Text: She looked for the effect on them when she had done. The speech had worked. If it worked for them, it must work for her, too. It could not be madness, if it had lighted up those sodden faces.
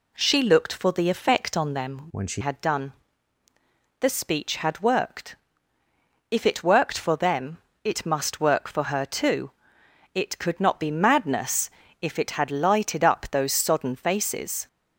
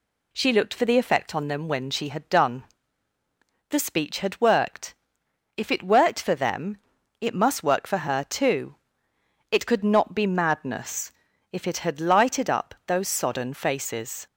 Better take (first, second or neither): second